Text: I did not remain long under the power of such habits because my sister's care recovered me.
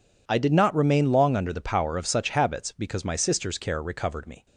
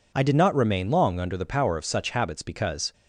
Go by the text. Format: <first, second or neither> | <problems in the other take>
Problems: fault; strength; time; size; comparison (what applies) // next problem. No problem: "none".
first | stops before "my sister's care recovered me"; at 2.9 s